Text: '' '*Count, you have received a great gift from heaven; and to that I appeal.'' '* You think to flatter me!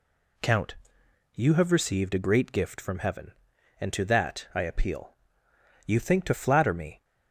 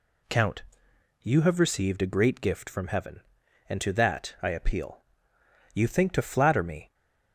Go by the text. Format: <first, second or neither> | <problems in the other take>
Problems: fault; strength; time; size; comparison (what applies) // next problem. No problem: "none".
neither | none